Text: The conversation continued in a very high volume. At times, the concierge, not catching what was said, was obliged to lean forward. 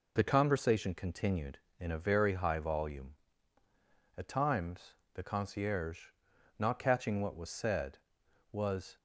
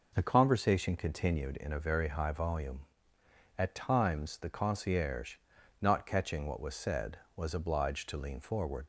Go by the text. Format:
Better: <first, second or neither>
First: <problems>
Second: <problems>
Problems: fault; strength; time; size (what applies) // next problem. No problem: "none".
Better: second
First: stops before "obliged to lean forward"; at 8.9 s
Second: none